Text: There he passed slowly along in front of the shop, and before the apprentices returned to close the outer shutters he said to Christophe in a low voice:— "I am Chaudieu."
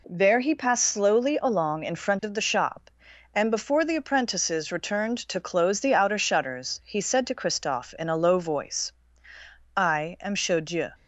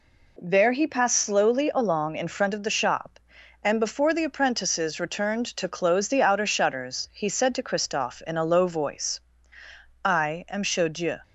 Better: neither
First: none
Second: none

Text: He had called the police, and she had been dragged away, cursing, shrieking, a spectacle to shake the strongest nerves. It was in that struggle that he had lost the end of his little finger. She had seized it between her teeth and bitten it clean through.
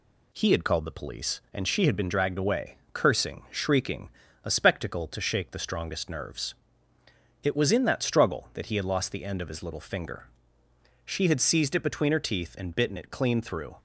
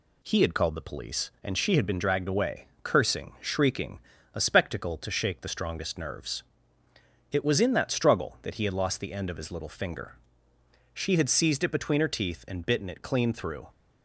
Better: neither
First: none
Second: none

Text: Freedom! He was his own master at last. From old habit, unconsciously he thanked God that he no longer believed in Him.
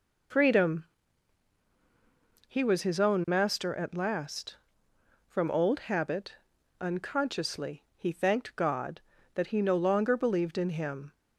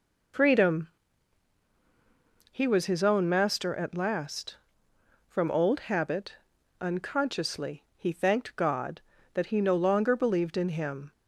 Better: neither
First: none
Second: none

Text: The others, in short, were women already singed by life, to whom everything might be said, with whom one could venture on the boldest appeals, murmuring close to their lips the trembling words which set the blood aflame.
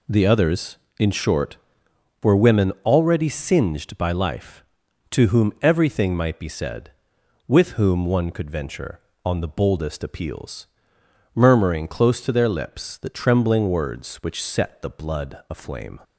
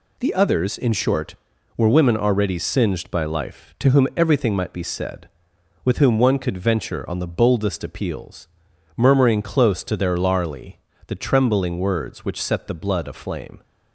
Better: first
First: none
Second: says "larly" for "lips"; at 10.1 s

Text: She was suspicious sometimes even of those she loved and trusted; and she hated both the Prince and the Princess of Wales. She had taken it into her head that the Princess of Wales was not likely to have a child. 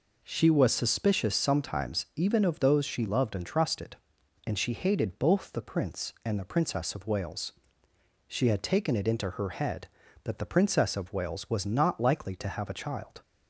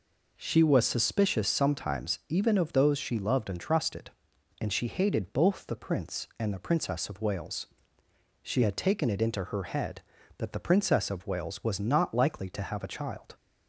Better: neither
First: none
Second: none

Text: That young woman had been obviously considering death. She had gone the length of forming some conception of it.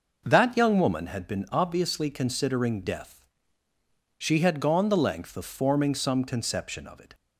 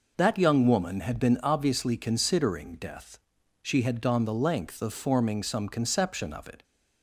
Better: neither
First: none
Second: none

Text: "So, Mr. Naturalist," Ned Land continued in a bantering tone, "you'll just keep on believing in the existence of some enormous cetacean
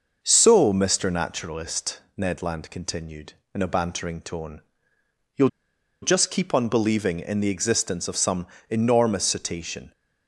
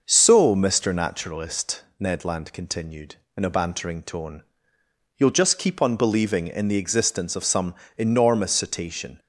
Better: second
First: pauses between "you'll" and "just"; noticeable; at 5.4 s; 0.54 s long // pauses between "some" and "enormous"; slight; at 8.4 s; 0.22 s long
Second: pauses between "some" and "enormous"; slight; at 7.7 s; 0.22 s long

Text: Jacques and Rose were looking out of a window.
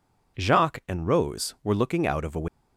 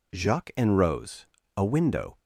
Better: first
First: none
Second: skips "were looking out of"; at 1.4 s

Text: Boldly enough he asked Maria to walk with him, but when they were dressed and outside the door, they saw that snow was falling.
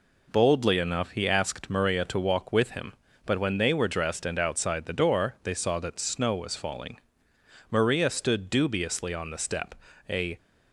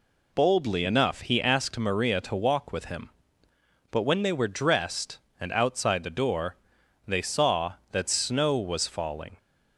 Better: second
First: goes on to say "Maria stood dubiously on the step a"; strong; from 7.6 s on; 2.6 s long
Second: none

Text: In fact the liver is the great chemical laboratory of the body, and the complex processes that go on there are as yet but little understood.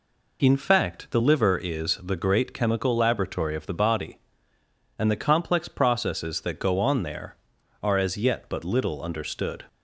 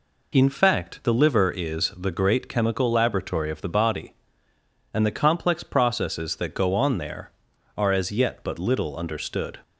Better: neither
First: none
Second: none

